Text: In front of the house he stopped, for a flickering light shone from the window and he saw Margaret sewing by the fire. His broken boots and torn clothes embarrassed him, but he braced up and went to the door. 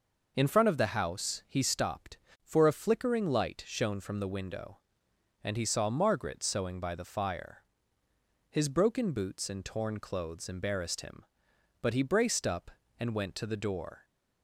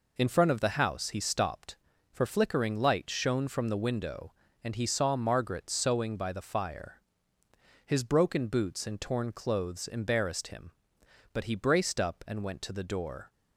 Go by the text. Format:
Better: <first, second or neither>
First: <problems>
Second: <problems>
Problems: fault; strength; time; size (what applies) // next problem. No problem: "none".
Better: first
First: none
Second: skips "a"; at 2.2 s